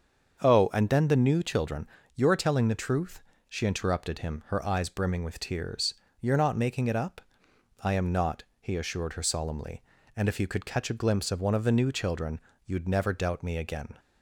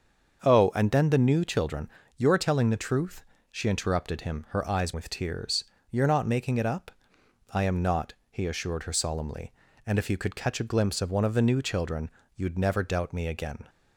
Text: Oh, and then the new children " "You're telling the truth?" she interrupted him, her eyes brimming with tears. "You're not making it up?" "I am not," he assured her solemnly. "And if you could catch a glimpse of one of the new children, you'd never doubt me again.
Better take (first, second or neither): first